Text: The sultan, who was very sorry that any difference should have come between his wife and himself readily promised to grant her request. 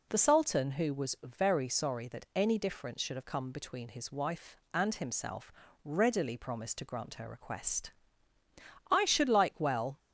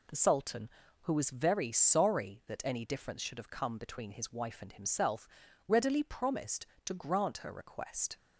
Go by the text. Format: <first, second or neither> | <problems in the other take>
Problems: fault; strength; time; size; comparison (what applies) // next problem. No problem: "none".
second | pauses between "himself" and "readily"; slight; at 5.5 s; 0.32 s long; also in the second // goes on to say "I should like well"; noticeable; from 8.9 s on; 1.0 s long